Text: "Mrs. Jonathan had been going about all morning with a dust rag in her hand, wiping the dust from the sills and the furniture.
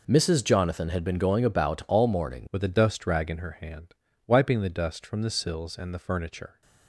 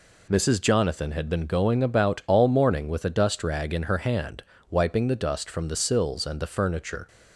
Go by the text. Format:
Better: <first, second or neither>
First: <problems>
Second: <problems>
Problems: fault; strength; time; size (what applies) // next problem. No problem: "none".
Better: second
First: changes voice at "with"; from 2.4 s on; 4.2 s long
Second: none